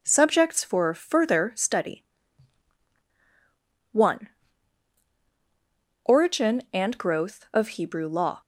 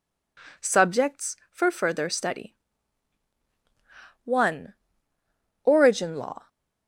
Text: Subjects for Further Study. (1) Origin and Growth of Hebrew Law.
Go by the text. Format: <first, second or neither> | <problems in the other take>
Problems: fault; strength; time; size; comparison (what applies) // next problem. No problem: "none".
first | skips "and Growth of Hebrew"; at 6.1 s